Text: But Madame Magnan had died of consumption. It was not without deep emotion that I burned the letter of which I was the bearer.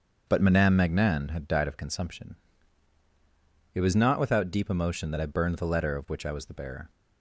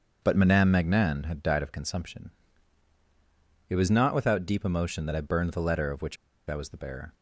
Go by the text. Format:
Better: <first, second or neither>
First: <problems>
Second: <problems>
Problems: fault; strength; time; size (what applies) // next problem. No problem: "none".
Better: first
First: starts louder than the rest; until 1.3 s; 7 dB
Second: starts louder than the rest; until 1.2 s; 7 dB // pauses between "which" and "I"; slight; at 6.1 s; 0.33 s long